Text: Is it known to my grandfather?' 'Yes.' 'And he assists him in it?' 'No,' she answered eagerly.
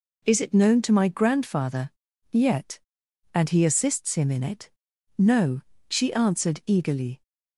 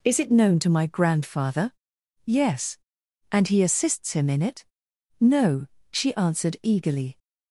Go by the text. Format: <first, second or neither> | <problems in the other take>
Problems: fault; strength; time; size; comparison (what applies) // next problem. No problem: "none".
second | says "Yet" for "Yes"; at 2.3 s